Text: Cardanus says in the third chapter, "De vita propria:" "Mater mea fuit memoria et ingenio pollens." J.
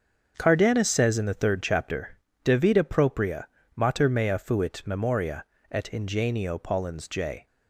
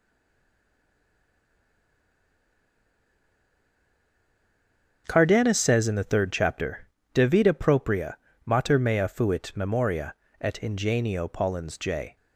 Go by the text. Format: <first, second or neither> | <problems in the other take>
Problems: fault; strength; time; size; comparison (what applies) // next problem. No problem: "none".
first | stays silent before the first word; strong; until 5.0 s; 5.0 s long // starts louder than the rest; until 6.0 s; 6.5 dB; also in the first // pauses between "memoria" and "et"; slight; at 10.1 s; 0.26 s long; slight in the first